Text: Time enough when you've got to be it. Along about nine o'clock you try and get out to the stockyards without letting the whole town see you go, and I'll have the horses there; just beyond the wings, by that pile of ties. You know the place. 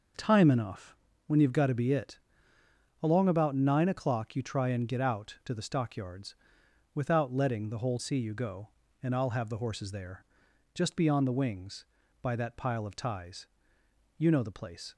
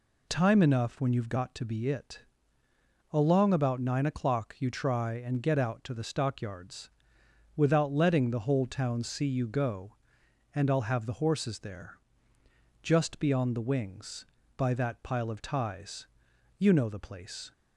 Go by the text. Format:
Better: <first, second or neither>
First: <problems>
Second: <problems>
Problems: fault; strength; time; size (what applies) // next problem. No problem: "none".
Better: second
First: pauses between "enough" and "when"; slight; at 0.9 s; 0.32 s long // pauses between "stockyards" and "without"; noticeable; at 6.3 s; 0.60 s long // skips "town"; at 7.9 s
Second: pauses between "stockyards" and "without"; noticeable; at 6.8 s; 0.66 s long